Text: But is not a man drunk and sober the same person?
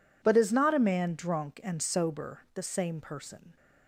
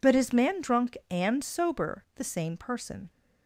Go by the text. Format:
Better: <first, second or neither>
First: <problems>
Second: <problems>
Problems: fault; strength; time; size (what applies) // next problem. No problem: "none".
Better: first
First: none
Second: skips "not a"; at 0.3 s